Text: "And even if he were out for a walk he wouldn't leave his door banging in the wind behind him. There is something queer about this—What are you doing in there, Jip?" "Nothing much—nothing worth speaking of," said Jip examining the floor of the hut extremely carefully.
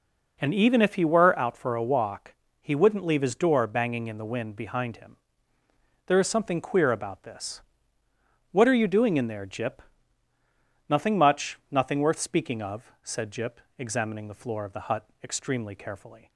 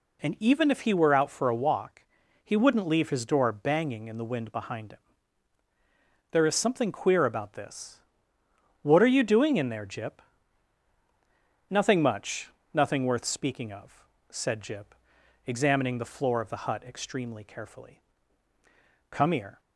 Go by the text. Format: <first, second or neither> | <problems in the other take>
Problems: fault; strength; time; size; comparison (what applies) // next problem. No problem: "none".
first | pauses between "walk" and "he"; at 2.0 s; 0.40 s long; slight in the first // pauses between "Jip" and "examining"; noticeable; at 14.9 s; 0.50 s long; slight in the first // goes on to say "Come here"; from 19.0 s on; 0.50 s long